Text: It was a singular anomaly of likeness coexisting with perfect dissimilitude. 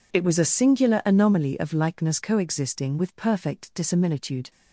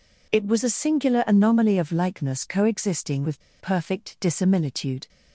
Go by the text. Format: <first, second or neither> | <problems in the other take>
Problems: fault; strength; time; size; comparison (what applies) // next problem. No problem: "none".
first | pauses between "with" and "perfect"; slight; at 3.4 s; 0.18 s long